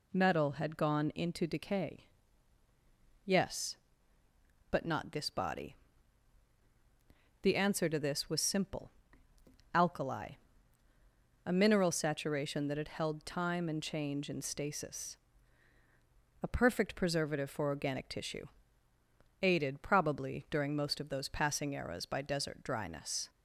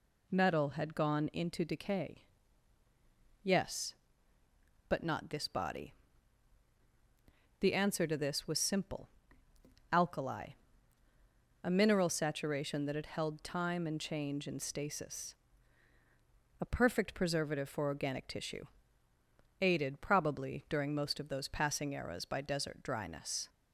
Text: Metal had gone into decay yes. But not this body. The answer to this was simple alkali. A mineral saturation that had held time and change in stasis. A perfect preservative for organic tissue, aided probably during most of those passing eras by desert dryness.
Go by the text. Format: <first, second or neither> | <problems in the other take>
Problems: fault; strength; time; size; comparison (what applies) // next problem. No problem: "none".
neither | pauses between "decay" and "yes"; the same in both // pauses between "simple" and "alkali"; noticeable; the same in both